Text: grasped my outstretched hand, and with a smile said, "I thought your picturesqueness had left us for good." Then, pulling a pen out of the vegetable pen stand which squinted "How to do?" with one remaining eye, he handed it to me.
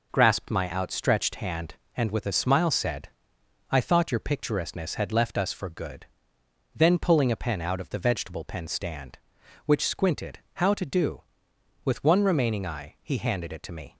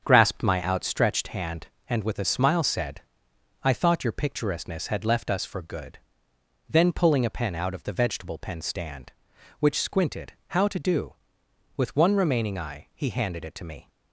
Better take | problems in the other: first | starts louder than the rest; strong; until 1.0 s; 7 dB // pauses between "squinted" and "How"; slight; at 10.3 s; 0.16 s long; slight in the first

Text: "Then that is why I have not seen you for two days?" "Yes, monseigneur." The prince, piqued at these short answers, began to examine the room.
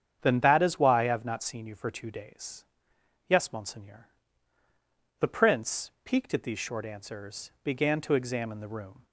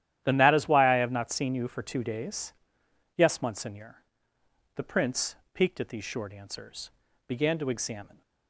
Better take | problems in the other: first | starts louder than the rest; strong; until 1.2 s; 11.5 dB; strong in the first // stops before "the room"; at 8.2 s

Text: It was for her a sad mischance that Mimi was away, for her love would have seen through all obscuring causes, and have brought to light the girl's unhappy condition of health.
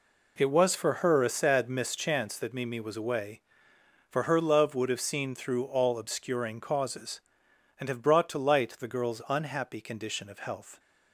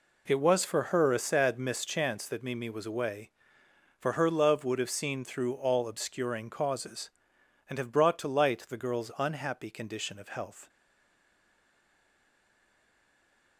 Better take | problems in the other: first | stays silent after the last word; strong; from 10.6 s on; 2.9 s long

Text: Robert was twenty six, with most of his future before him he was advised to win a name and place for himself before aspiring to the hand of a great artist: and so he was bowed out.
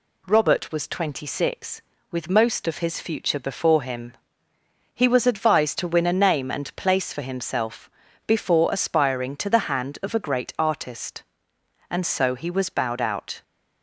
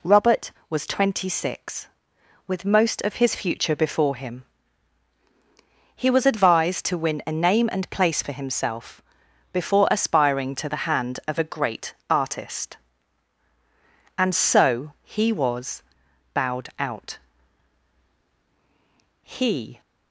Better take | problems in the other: first | pauses between "him" and "he"; strong; at 4.4 s; 1.5 s long; noticeable in the first // pauses between "himself" and "before"; noticeable; at 9.0 s; 0.50 s long; slight in the first // pauses between "great" and "artist"; slight; at 11.9 s; 0.16 s long // pauses between "was" and "bowed"; noticeable; at 15.8 s; 0.50 s long // goes on to say "He"; from 19.2 s on; 0.58 s long

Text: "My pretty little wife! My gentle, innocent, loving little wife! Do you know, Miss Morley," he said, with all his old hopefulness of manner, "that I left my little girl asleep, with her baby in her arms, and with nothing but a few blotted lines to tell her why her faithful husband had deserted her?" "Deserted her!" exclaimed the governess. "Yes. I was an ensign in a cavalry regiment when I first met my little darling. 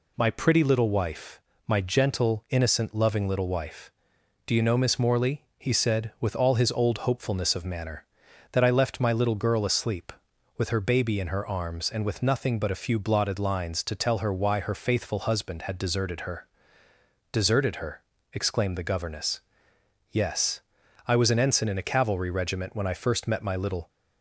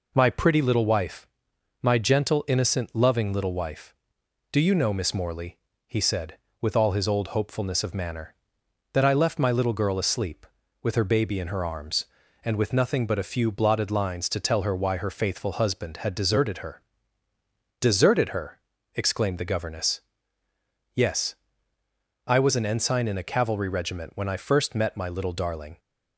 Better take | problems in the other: second | stops before "darling"; at 23.8 s

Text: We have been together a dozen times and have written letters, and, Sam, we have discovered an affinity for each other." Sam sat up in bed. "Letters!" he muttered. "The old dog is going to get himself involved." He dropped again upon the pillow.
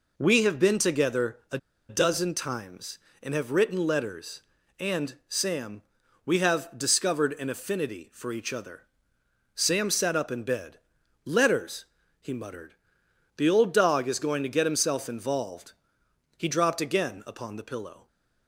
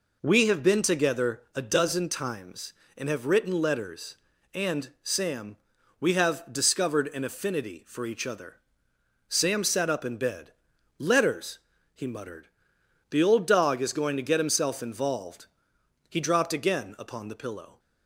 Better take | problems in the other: second | pauses between "a" and "dozen"; slight; at 1.5 s; 0.31 s long

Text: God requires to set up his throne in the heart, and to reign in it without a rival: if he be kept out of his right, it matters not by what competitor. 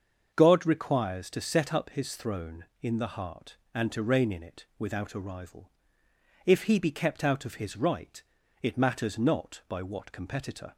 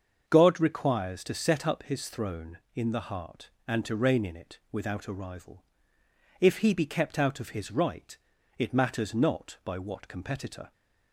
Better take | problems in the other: neither | starts louder than the rest; the same in both

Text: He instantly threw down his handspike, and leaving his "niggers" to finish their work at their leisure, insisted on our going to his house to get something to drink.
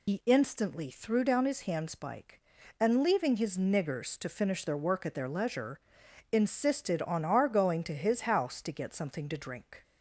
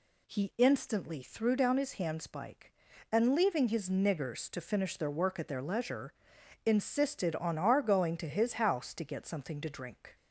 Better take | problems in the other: second | loses the start of "He"; at 0.0 s; 115 ms

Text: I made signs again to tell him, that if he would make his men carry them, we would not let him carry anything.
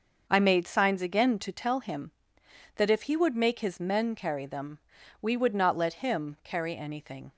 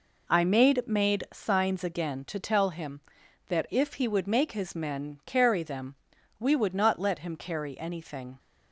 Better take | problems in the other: first | says "made" twice; at 0.8 s

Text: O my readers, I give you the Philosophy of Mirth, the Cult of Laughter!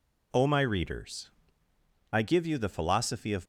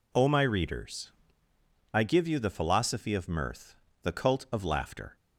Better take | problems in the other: second | stops before "Mirth the Cult of Laughter"; at 3.4 s

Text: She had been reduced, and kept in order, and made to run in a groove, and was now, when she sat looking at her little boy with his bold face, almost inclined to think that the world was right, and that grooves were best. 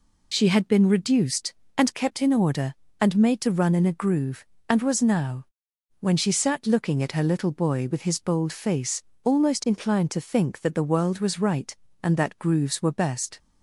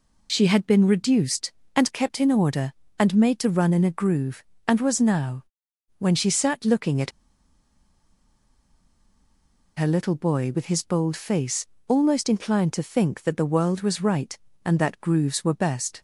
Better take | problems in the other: first | pauses between "at" and "her"; strong; at 7.1 s; 2.6 s long

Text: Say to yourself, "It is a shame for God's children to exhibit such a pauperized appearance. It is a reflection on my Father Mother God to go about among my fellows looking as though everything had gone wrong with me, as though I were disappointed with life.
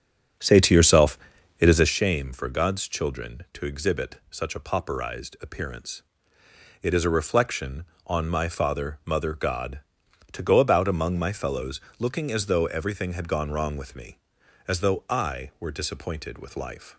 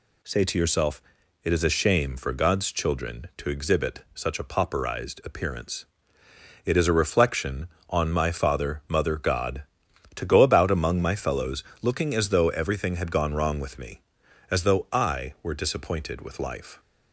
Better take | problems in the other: second | starts louder than the rest; strong; until 2.0 s; 8 dB // pauses between "fellows" and "looking"; slight; at 11.8 s; 0.18 s long; slight in the second

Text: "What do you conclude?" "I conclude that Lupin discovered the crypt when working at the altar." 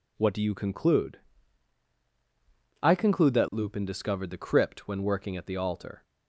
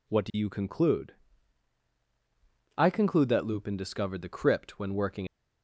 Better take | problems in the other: first | stops before "at the altar"; at 5.2 s

